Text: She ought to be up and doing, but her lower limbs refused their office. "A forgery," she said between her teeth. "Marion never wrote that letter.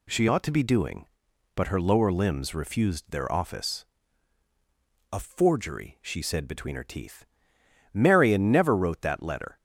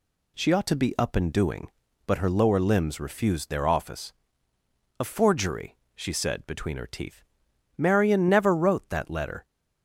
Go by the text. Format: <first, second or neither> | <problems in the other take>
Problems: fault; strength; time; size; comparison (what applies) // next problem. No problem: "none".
second | skips "up and"; at 0.6 s